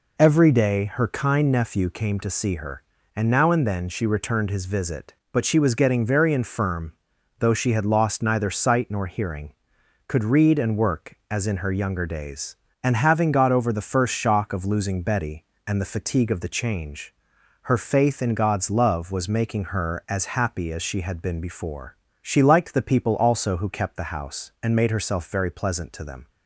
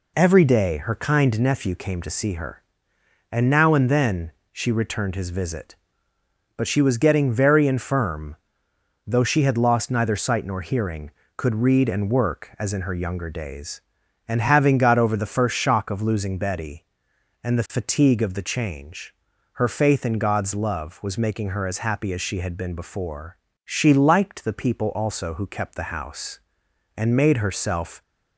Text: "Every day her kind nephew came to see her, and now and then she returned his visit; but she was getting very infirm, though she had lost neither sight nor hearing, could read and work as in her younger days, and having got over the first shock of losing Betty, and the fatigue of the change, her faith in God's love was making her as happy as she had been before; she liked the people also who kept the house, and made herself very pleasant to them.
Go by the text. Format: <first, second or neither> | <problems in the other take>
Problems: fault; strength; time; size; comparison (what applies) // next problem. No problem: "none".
first | pauses between "then" and "she"; slight; at 4.3 s; 0.20 s long // stops before "very pleasant to them"; at 28.0 s